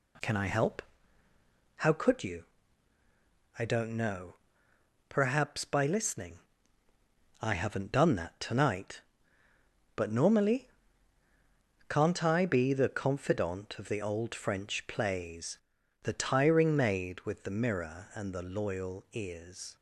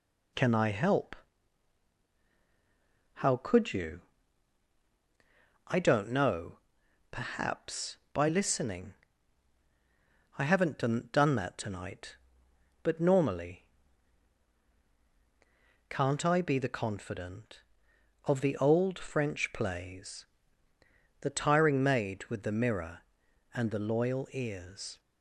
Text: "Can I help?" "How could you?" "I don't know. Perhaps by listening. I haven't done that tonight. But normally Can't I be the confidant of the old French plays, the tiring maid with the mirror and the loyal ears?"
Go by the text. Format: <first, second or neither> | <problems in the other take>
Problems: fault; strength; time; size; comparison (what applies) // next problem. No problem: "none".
first | says "done" twice; at 11.1 s // pauses between "normally" and "Can't"; strong; at 13.6 s; 2.2 s long; also in the first